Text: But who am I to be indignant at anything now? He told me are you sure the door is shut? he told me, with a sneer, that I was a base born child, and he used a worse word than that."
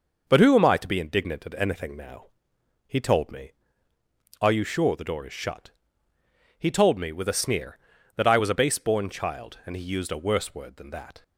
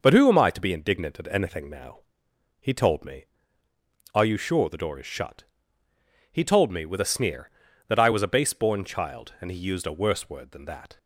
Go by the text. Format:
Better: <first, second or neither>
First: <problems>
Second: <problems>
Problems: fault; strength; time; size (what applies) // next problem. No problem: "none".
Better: neither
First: none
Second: none